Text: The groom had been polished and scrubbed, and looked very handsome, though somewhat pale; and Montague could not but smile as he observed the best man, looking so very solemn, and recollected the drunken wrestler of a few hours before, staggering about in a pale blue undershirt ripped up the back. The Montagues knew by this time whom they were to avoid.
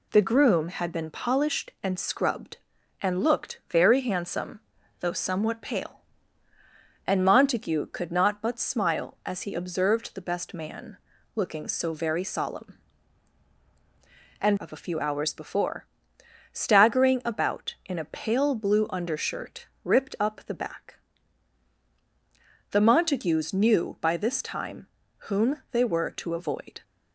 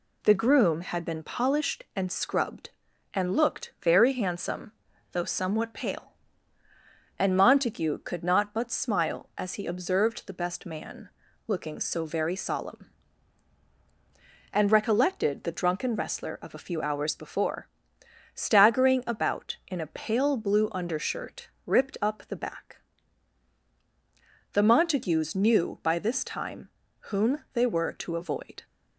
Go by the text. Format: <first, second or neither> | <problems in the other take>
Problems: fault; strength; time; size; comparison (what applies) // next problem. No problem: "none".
second | skips "recollected the drunken wrestler"; at 14.5 s // pauses between "undershirt" and "ripped"; slight; at 19.6 s; 0.16 s long; slight in the second // pauses between "time" and "whom"; at 24.8 s; 0.40 s long; also in the second